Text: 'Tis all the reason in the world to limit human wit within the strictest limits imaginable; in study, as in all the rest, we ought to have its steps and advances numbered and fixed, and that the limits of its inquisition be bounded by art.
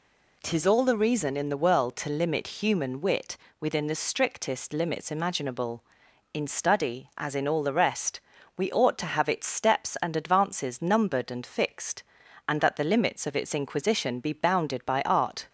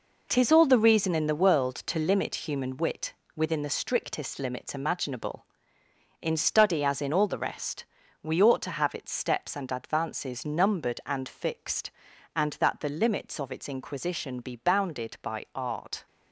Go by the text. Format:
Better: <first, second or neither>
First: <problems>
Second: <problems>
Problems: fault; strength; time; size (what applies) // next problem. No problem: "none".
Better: first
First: pauses between "wit" and "within"; slight; at 3.3 s; 0.22 s long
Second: gets quieter; strong; throughout; 9 dB // pauses between "wit" and "within"; slight; at 3.1 s; 0.24 s long